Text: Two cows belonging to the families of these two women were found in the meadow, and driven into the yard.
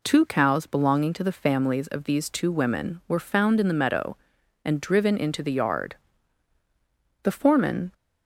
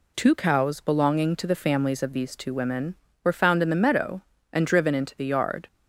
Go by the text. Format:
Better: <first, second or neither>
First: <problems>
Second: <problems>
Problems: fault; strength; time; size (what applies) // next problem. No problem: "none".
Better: second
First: goes on to say "The foreman"; noticeable; from 7.2 s on; 0.70 s long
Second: none